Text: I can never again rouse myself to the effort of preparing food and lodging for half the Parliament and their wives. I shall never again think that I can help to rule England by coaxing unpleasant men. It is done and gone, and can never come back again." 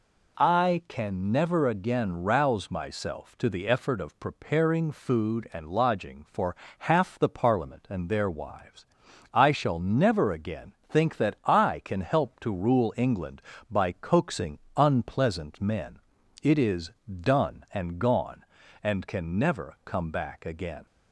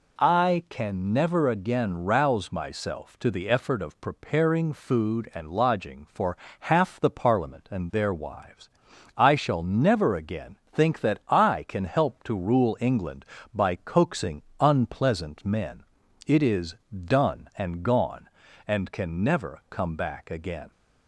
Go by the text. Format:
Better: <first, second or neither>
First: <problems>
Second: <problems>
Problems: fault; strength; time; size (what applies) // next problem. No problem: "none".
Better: neither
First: pauses between "for" and "half"; slight; at 6.5 s; 0.22 s long // pauses between "again" and "think"; slight; at 10.7 s; 0.16 s long // pauses between "coaxing" and "unpleasant"; slight; at 14.5 s; 0.16 s long // pauses between "is" and "done"; slight; at 16.9 s; 0.30 s long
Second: pauses between "for" and "half"; slight; at 6.3 s; 0.22 s long // pauses between "again" and "think"; slight; at 10.5 s; 0.16 s long // pauses between "coaxing" and "unpleasant"; slight; at 14.4 s; 0.16 s long // pauses between "is" and "done"; slight; at 16.7 s; 0.30 s long